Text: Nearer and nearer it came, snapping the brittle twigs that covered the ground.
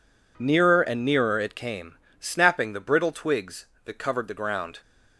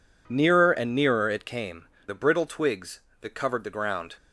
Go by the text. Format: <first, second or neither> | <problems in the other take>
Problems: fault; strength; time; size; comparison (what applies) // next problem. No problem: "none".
first | skips "snapping"; at 1.9 s